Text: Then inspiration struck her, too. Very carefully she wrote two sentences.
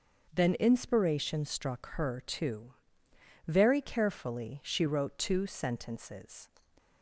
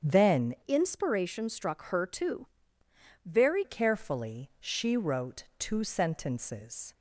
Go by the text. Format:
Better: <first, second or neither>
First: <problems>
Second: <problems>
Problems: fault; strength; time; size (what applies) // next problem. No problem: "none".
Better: first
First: starts louder than the rest; until 1.3 s; 6.5 dB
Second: starts louder than the rest; strong; until 1.1 s; 8 dB // changes voice from "inspiration" to "Very"; from 0.6 to 3.6 s; 3.0 s long